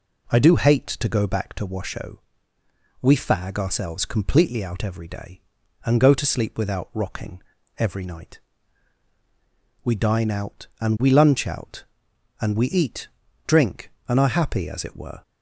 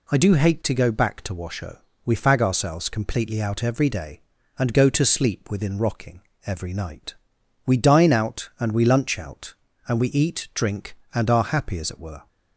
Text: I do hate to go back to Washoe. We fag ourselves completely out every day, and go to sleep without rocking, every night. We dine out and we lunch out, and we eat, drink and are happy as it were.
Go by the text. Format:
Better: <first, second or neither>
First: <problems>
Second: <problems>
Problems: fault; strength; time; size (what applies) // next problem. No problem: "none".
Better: first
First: none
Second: says "within" for "without"; at 5.4 s